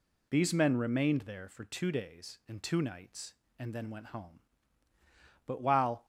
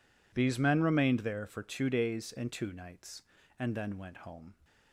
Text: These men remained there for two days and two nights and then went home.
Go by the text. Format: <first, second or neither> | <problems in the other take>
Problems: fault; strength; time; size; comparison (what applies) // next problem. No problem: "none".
second | goes on to say "But while"; from 5.4 s on; 0.58 s long